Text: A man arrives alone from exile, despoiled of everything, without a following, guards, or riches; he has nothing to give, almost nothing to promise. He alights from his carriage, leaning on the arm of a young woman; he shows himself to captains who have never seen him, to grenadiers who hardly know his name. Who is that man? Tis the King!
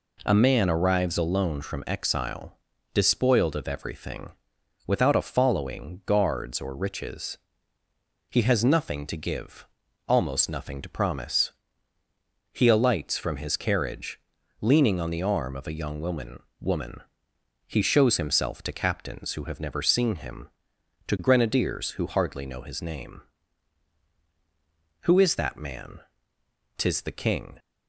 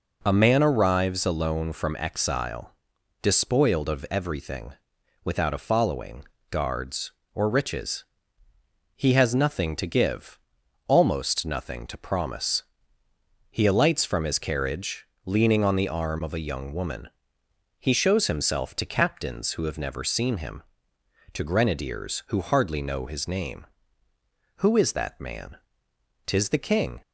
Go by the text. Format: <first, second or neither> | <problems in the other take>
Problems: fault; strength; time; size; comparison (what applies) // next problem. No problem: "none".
second | says "woman" twice; at 16.5 s